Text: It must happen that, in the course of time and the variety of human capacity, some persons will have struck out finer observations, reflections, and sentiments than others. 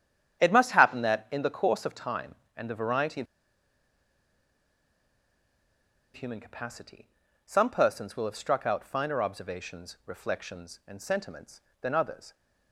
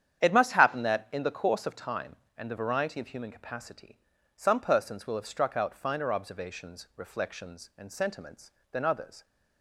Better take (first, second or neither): second